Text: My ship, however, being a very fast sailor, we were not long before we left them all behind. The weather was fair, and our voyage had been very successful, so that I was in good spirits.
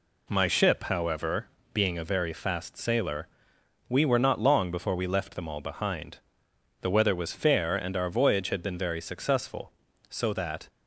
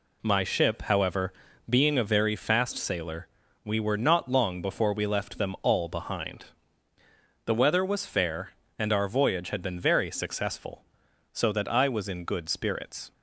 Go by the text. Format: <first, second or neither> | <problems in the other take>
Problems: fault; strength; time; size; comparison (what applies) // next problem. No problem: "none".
second | stops before "I was in good spirits"; at 10.6 s